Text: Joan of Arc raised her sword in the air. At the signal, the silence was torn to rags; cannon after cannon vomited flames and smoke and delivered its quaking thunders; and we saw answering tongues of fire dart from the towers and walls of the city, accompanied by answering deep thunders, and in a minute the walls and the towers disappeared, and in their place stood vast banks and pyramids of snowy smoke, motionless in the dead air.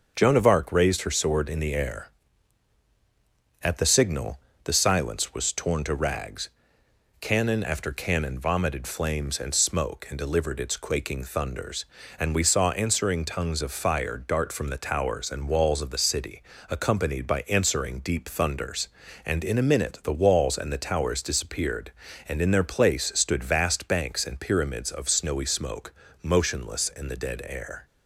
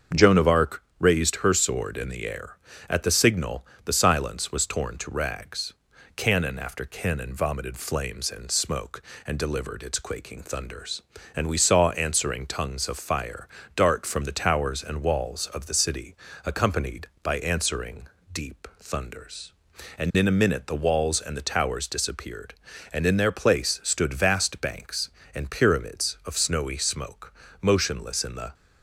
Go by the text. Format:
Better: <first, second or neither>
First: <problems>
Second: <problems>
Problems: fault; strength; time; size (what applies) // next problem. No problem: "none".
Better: first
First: starts louder than the rest; until 1.1 s; 6.5 dB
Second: starts louder than the rest; until 1.3 s; 7 dB // pauses between "Arc" and "raised"; slight; at 0.8 s; 0.16 s long // pauses between "fire" and "dart"; slight; at 13.4 s; 0.26 s long // pauses between "answering" and "deep"; slight; at 18.0 s; 0.28 s long // stops before "dead air"; at 28.5 s